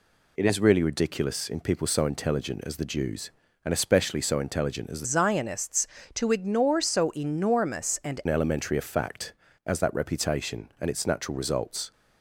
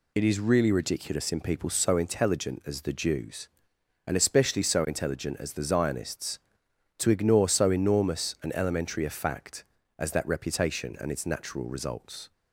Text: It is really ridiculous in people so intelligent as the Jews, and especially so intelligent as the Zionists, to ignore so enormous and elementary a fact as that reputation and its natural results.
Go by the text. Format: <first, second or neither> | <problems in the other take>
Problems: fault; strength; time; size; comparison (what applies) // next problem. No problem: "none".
second | changes voice from "Zionists" to "and"; from 5.0 to 8.2 s; 3.2 s long